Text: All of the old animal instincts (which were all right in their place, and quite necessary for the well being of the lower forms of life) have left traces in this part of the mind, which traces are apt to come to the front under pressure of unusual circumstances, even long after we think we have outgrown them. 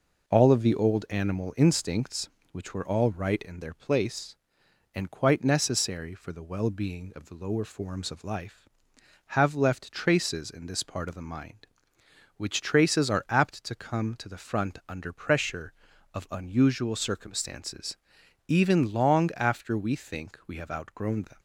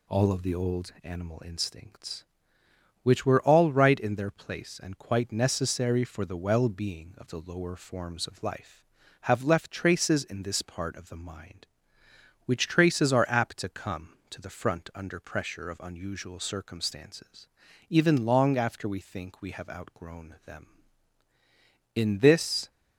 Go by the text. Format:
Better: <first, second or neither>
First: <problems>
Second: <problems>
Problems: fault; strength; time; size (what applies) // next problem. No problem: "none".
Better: first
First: none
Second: goes on to say "In this"; noticeable; from 21.9 s on; 0.74 s long